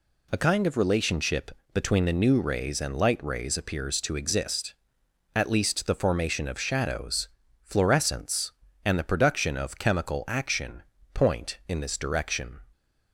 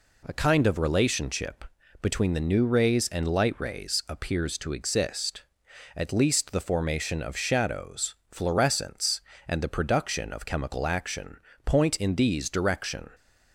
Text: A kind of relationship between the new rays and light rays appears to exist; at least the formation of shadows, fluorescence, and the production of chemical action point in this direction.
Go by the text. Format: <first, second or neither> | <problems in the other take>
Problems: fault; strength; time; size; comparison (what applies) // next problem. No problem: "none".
first | pauses between "relationship" and "between"; slight; at 1.6 s; 0.34 s long; slight in the first // pauses between "action" and "point"; slight; at 11.3 s; 0.26 s long; slight in the first // says "these" for "this"; at 12.1 s